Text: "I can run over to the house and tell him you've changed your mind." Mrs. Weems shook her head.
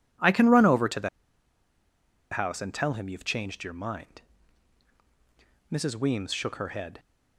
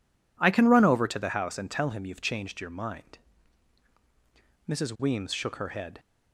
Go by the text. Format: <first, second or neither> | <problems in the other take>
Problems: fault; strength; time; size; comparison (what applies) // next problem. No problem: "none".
second | pauses between "the" and "house"; at 1.0 s; 1.2 s long